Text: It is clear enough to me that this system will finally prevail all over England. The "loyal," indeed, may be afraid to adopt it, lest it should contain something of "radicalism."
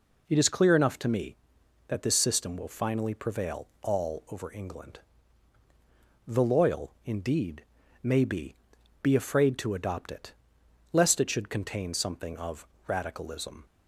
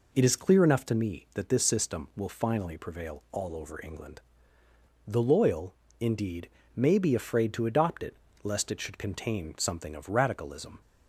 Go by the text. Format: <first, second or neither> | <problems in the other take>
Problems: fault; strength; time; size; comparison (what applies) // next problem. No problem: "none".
second | pauses between "prevail" and "all"; slight; at 3.6 s; 0.16 s long // says "be" twice; at 9.0 s // pauses between "of" and "radicalism"; slight; at 12.6 s; 0.22 s long